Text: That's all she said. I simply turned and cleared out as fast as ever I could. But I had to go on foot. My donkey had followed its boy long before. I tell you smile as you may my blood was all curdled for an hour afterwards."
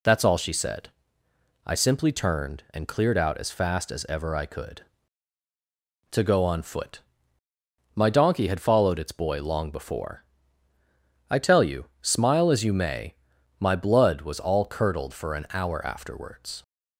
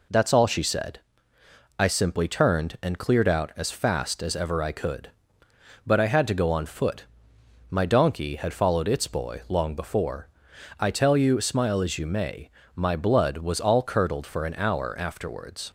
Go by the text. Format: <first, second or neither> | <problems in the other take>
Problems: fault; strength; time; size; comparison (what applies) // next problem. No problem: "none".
second | skips "But I had"; at 5.4 s // pauses between "may" and "my"; noticeable; at 13.1 s; 0.46 s long; slight in the second